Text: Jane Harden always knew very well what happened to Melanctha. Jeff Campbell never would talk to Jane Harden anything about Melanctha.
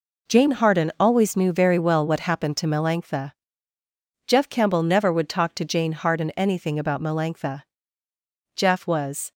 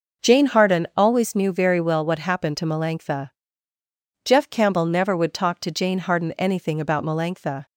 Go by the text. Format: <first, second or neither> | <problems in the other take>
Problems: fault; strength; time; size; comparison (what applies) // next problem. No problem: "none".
second | goes on to say "Jeff was"; noticeable; from 8.5 s on; 0.76 s long